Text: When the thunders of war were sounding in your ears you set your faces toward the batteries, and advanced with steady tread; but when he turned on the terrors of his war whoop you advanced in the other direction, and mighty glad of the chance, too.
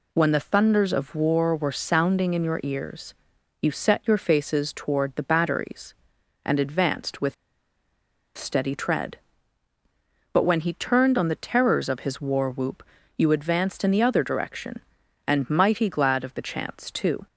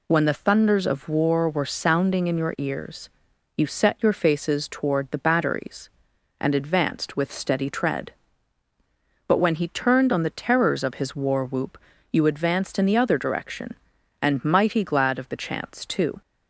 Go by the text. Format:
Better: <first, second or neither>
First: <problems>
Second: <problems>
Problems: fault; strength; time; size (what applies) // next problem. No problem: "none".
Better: second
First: pauses between "ears" and "you"; noticeable; at 3.1 s; 0.48 s long // pauses between "with" and "steady"; at 7.3 s; 1.0 s long // pauses between "whoop" and "you"; slight; at 12.8 s; 0.36 s long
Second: pauses between "ears" and "you"; noticeable; at 3.0 s; 0.48 s long // pauses between "whoop" and "you"; slight; at 11.7 s; 0.36 s long